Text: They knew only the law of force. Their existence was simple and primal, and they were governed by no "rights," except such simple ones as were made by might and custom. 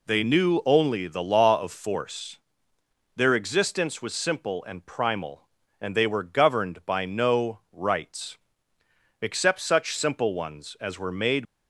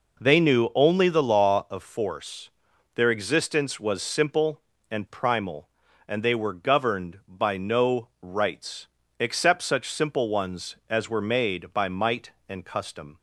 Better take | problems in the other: second | stops before "by might and custom"; at 11.4 s

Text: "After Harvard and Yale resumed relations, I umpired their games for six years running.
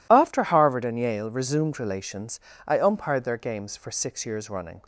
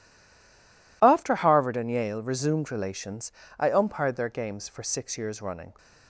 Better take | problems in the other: first | stays silent before the first word; until 1.0 s; 1.0 s long

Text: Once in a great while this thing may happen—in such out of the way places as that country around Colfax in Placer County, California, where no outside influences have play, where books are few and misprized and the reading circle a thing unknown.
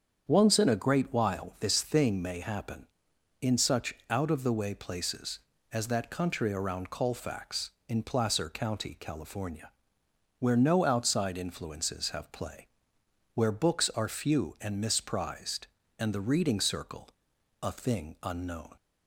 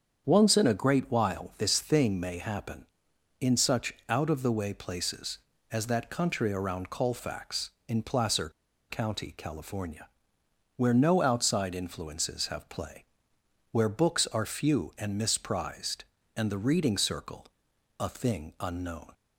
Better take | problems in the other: first | starts louder than the rest; strong; until 1.3 s; 8 dB; strong in the first // pauses between "such" and "out"; slight; at 3.9 s; 0.16 s long; slight in the first // pauses between "Placer" and "County"; at 8.4 s; 0.40 s long // pauses between "circle" and "a"; noticeable; at 17.4 s; 0.54 s long; noticeable in the first

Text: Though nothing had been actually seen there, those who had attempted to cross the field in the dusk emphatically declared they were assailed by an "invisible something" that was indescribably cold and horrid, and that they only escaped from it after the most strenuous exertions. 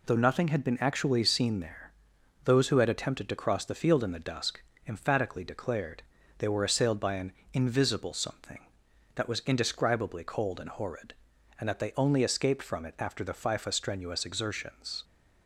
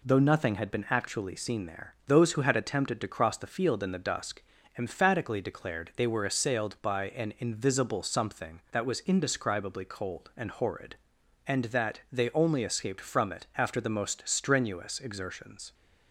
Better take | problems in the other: second | pauses between "dusk" and "emphatically"; slight; at 4.5 s; 0.28 s long; slight in the second // pauses between "declared" and "they"; at 6.0 s; 0.38 s long // pauses between "an" and "invisible"; slight; at 7.3 s; 0.22 s long // says "fifa" for "most"; at 13.3 s

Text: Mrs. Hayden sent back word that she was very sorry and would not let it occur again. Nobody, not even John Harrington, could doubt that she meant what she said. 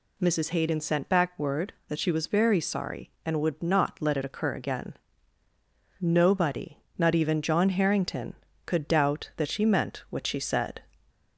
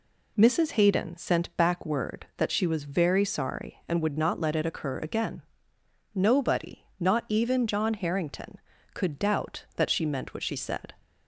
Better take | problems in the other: neither | none

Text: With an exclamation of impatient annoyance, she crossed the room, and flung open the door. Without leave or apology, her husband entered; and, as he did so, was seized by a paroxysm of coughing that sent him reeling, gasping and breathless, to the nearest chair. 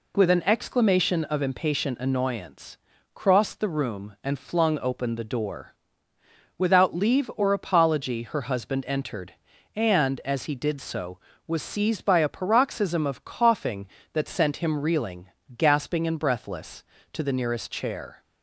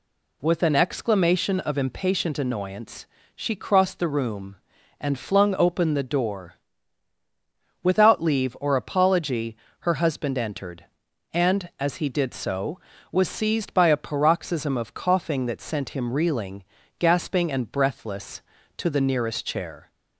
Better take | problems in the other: second | skips "she"; at 2.9 s

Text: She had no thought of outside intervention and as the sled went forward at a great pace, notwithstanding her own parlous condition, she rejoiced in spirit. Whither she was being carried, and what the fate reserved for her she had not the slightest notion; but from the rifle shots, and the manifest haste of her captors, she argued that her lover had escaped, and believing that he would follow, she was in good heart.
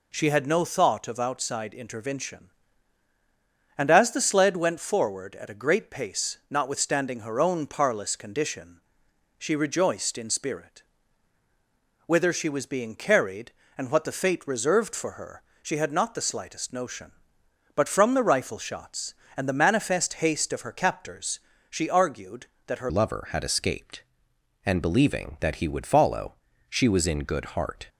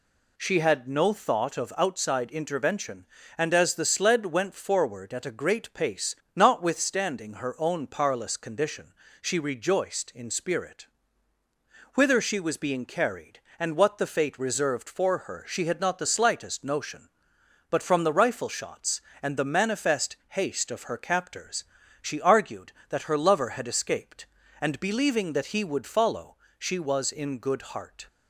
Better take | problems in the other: second | pauses between "her" and "she"; slight; at 15.4 s; 0.22 s long // changes voice at "lover"; from 22.8 s on; 5.0 s long

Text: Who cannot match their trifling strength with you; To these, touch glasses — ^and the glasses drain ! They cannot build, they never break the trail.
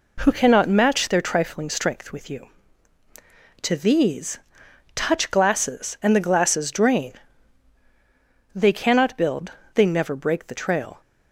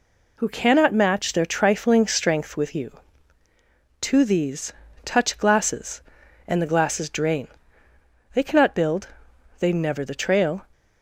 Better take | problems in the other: first | skips "break"; at 10.0 s

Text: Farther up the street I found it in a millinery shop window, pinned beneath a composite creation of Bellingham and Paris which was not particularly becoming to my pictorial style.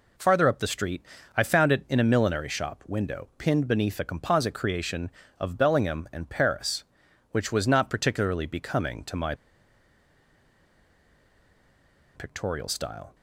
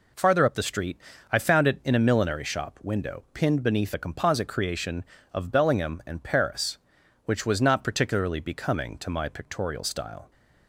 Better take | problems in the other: second | pauses between "street" and "I"; slight; at 1.0 s; 0.32 s long; slight in the second // pauses between "my" and "pictorial"; strong; at 9.3 s; 2.8 s long

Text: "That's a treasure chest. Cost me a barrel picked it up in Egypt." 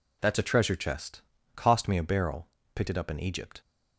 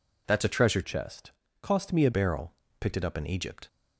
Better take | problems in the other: first | changes voice from "chest" to "a"; from 0.8 to 2.1 s; 1.3 s long // pauses between "barrel" and "picked"; slight; at 2.5 s; 0.26 s long; slight in the first

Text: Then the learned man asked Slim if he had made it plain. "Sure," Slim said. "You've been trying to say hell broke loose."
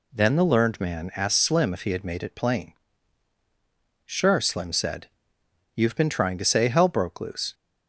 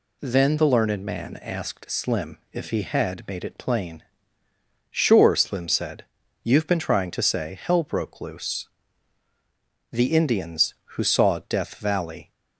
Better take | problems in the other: first | goes on to say "The Indians who saw Death Valley"; strong; from 9.9 s on; 2.4 s long

